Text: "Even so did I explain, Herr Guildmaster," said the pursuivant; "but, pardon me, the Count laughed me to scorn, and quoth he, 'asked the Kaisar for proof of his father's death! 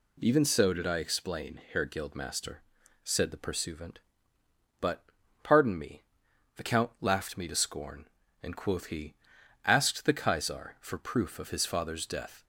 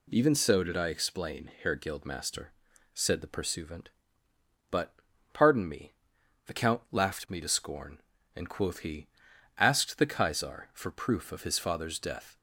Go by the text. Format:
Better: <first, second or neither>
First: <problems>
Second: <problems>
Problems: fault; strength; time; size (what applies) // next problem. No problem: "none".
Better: neither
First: none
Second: none